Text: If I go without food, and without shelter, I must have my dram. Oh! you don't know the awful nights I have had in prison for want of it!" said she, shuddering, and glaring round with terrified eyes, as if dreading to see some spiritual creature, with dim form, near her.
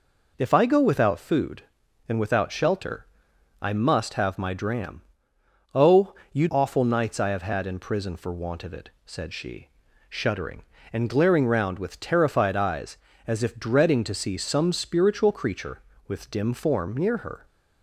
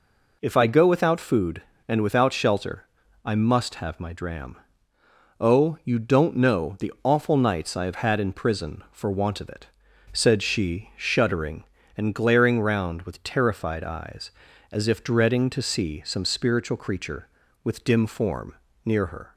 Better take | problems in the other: second | skips "don't know the"; at 6.4 s

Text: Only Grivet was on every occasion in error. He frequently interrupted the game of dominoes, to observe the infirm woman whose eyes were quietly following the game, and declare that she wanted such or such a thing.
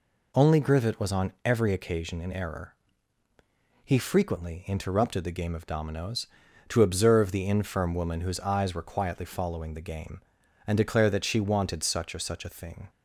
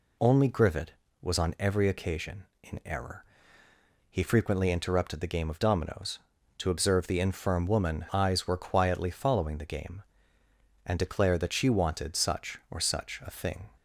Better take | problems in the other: first | skips "whose"; at 8.0 s

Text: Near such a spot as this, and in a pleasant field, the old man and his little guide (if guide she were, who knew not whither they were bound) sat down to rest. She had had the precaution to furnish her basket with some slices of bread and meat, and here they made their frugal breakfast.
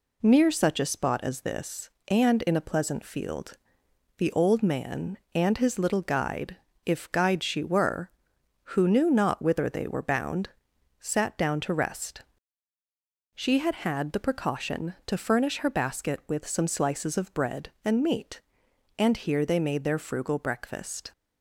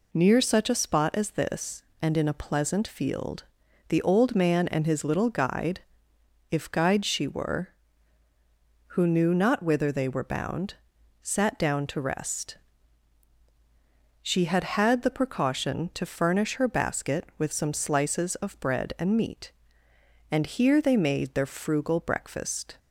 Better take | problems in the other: neither | none

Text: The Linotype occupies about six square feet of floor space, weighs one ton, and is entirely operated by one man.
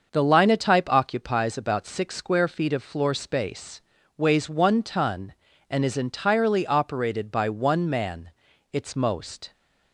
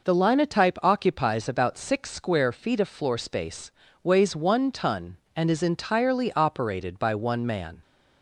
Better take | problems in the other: second | starts louder than the rest; until 1.1 s; 6.5 dB // goes on to say "Its most"; noticeable; from 8.7 s on; 0.80 s long

